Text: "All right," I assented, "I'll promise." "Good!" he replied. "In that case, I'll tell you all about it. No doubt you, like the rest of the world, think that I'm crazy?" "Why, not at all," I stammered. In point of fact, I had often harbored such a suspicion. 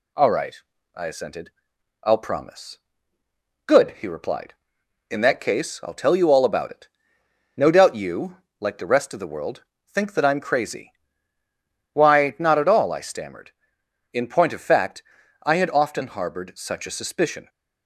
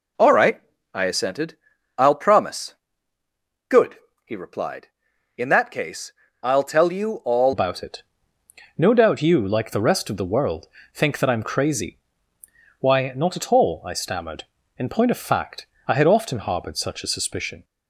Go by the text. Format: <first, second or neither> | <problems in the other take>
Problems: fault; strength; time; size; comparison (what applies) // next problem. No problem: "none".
first | changes voice at "about"; from 7.5 s on; 10.1 s long